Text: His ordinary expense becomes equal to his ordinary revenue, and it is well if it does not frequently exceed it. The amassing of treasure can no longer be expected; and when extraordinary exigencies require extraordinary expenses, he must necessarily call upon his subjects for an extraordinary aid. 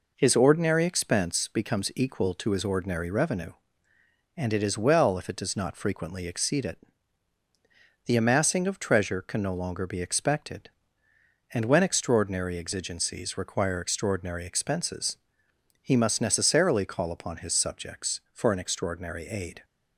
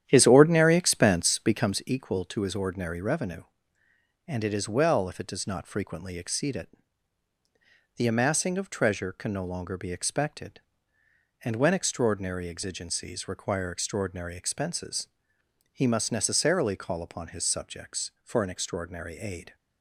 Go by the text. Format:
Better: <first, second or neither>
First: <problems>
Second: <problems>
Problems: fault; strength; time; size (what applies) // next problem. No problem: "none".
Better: first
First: none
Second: starts louder than the rest; strong; until 1.9 s; 10 dB